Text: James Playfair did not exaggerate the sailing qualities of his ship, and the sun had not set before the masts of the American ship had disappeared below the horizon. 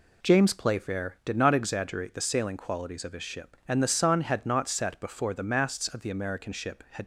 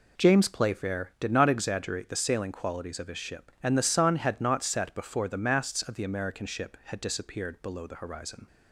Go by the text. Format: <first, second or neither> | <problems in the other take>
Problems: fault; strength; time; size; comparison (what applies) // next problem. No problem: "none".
second | stops before "disappeared below the horizon"; at 7.0 s